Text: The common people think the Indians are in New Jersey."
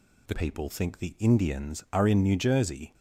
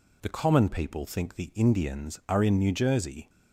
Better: second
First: skips "common"; at 0.3 s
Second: none

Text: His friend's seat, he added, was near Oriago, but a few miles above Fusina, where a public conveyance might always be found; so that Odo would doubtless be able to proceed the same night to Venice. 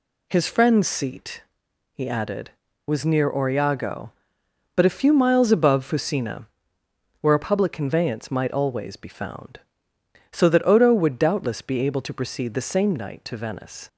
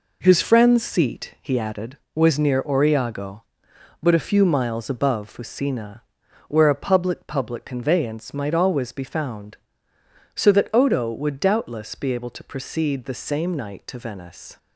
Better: first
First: none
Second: says "public" twice; at 7.2 s

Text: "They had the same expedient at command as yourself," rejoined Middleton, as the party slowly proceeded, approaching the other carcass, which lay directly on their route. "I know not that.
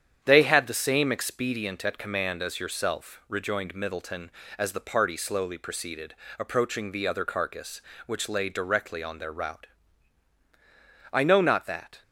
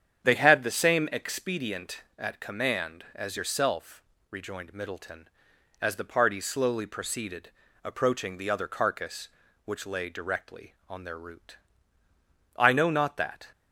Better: neither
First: starts louder than the rest; strong; until 1.2 s; 9 dB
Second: starts louder than the rest; strong; until 1.2 s; 8.5 dB

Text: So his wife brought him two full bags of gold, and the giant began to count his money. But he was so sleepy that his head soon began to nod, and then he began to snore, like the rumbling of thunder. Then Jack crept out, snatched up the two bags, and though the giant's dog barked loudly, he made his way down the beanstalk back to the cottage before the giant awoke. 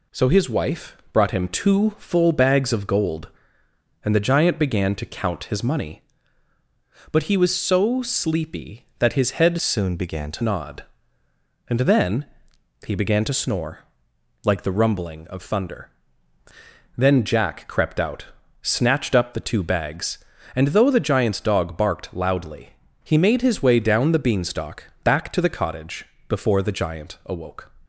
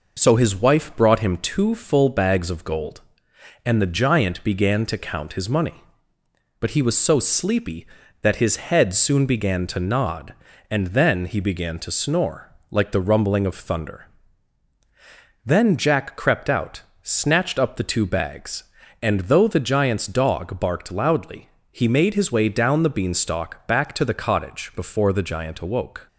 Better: second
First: pauses between "wife" and "brought"; slight; at 0.9 s; 0.16 s long // changes voice from "soon" to "to"; from 9.6 to 10.4 s; 0.8 s long // pauses between "then" and "he"; noticeable; at 12.2 s; 0.60 s long // pauses between "cottage" and "before"; slight; at 26.0 s; 0.24 s long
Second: none

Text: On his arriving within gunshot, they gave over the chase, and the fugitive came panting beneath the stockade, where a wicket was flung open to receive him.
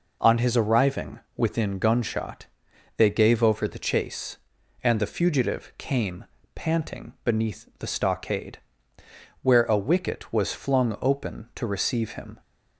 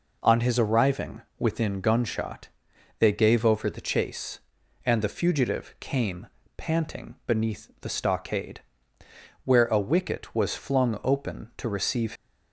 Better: first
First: pauses between "arriving" and "within"; slight; at 1.2 s; 0.16 s long // pauses between "came" and "panting"; slight; at 6.2 s; 0.30 s long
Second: pauses between "arriving" and "within"; slight; at 1.2 s; 0.16 s long // pauses between "came" and "panting"; slight; at 6.2 s; 0.30 s long // stops before "him"; at 12.1 s

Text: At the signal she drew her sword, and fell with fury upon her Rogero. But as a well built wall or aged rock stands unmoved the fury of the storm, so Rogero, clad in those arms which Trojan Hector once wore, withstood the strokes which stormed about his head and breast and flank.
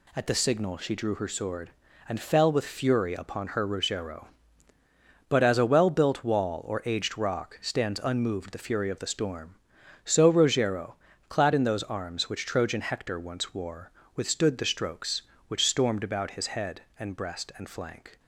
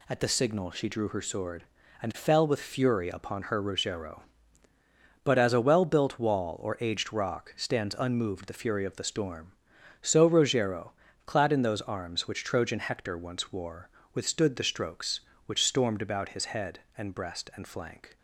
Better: neither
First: none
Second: none

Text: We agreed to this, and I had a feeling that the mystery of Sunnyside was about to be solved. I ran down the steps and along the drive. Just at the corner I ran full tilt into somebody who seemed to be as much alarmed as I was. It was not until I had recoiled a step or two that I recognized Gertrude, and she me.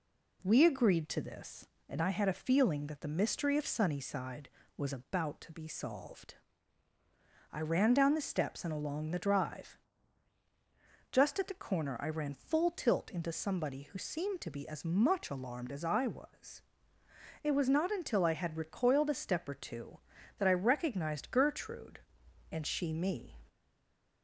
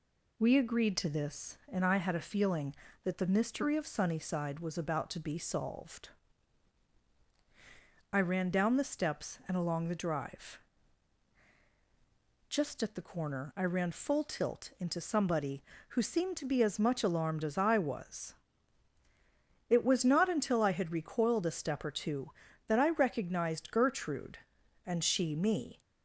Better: second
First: stays silent after the last word; slight; from 23.4 s on; 0.8 s long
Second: none

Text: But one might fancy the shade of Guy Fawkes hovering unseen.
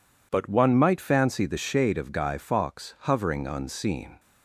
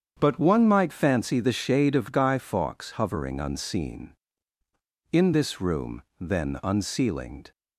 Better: first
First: none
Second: starts louder than the rest; strong; until 1.2 s; 8 dB // goes on to say "In this room then unceilinged"; strong; from 5.1 s on; 2.3 s long

